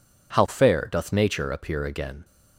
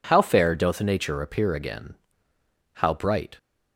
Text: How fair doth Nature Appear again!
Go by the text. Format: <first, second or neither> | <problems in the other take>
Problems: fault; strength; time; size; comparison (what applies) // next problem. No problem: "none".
first | goes on to say "How bright"; noticeable; from 2.7 s on; 0.64 s long